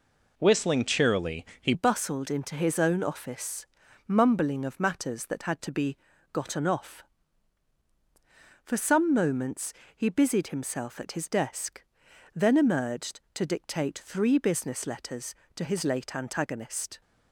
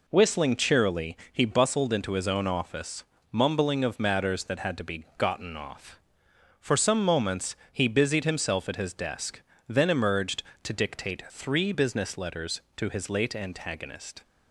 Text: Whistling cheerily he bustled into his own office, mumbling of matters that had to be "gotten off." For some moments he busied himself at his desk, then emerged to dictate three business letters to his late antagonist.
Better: second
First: pauses between "cheerily" and "he"; slight; at 1.4 s; 0.16 s long // changes voice at "bustled"; from 1.7 s on; 15.3 s long // pauses between "be" and "gotten"; slight; at 5.9 s; 0.36 s long // pauses between "moments" and "he"; slight; at 9.7 s; 0.24 s long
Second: pauses between "cheerily" and "he"; slight; at 1.1 s; 0.16 s long // pauses between "moments" and "he"; slight; at 7.5 s; 0.16 s long

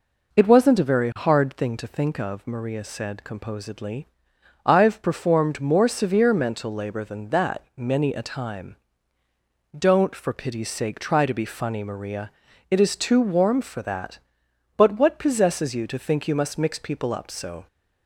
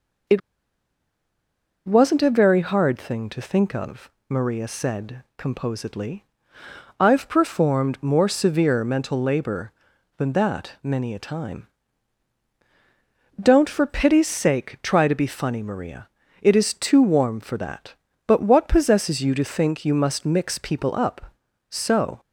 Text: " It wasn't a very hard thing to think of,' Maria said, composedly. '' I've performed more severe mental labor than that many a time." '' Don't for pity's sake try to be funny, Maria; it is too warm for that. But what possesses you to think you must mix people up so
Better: first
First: none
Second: pauses between "It" and "wasn't"; strong; at 0.4 s; 1.4 s long

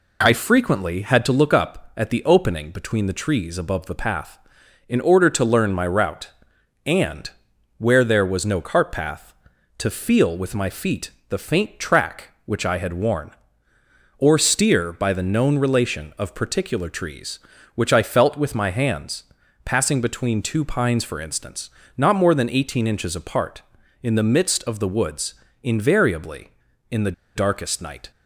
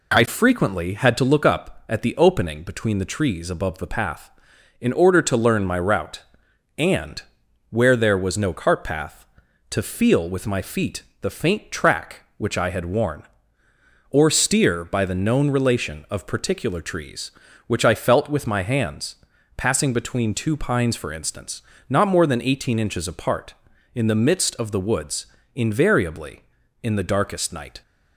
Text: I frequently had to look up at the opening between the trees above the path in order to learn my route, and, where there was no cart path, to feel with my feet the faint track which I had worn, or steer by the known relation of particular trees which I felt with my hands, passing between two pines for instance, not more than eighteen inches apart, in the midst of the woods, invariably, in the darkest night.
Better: second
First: pauses between "feet" and "the"; slight; at 11.0 s; 0.20 s long // pauses between "the" and "darkest"; slight; at 27.1 s; 0.23 s long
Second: pauses between "feet" and "the"; slight; at 11.0 s; 0.20 s long

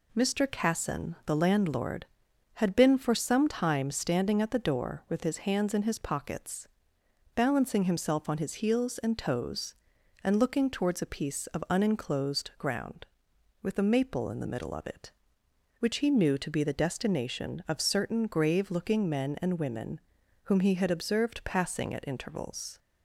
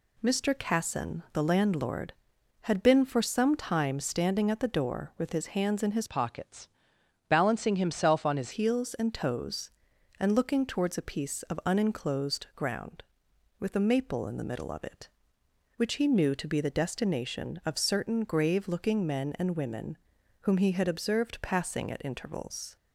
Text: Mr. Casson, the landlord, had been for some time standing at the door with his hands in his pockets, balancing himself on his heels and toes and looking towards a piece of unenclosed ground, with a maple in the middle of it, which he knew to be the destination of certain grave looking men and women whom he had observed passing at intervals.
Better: first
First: pauses between "women" and "whom"; at 20.0 s; 0.44 s long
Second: changes voice from "pockets" to "his"; from 6.0 to 8.5 s; 2.5 s long // pauses between "women" and "whom"; at 19.9 s; 0.44 s long

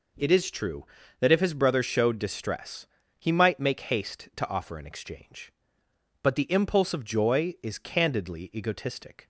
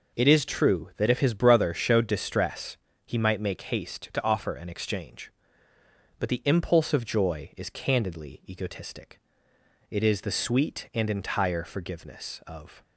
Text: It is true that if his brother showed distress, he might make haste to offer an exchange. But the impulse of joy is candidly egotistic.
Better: first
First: none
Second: goes on to say "It is the sweet and entire forgiveness of"; strong; from 9.8 s on; 2.9 s long

